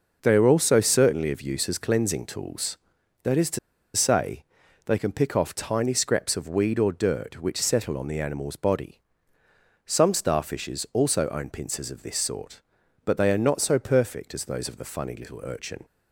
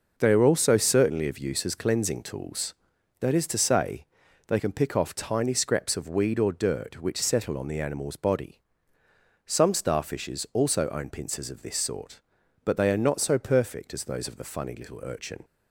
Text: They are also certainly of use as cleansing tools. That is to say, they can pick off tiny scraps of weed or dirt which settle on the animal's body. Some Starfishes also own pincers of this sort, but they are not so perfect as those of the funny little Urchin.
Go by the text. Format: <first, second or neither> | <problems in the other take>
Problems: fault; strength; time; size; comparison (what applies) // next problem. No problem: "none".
second | pauses between "to" and "say"; at 3.5 s; 0.37 s long